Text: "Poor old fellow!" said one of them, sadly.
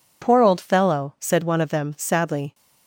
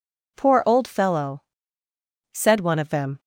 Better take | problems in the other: first | stops before "sadly"; at 3.1 s

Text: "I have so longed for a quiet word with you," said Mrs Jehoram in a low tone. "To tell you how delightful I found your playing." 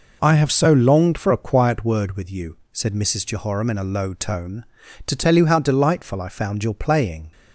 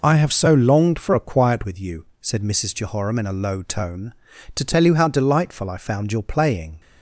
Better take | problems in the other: first | skips "word"; at 1.6 s

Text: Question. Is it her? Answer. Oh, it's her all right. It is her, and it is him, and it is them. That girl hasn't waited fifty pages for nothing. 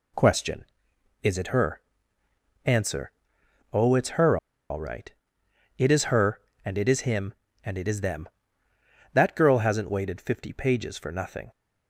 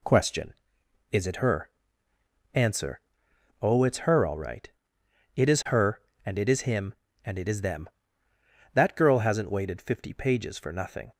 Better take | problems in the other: second | pauses between "her" and "all"; slight; at 4.3 s; 0.33 s long

